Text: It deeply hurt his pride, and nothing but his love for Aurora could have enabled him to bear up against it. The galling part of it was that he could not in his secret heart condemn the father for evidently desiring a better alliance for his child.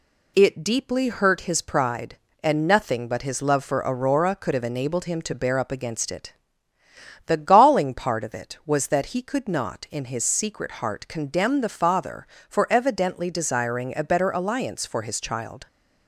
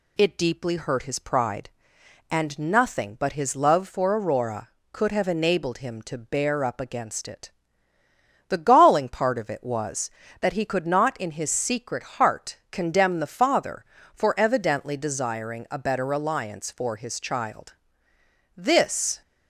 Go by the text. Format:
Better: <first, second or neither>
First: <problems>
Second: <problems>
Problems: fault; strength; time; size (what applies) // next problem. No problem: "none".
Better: first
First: none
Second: goes on to say "This"; noticeable; from 18.5 s on; 0.66 s long